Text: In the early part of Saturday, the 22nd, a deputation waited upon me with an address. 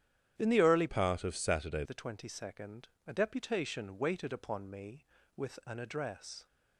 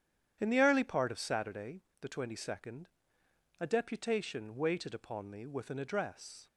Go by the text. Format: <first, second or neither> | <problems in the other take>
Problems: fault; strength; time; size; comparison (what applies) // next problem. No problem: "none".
second | starts louder than the rest; strong; until 1.3 s; 10.5 dB; strong in the second // changes voice from "part" to "Saturday"; from 0.8 to 1.8 s; 1.0 s long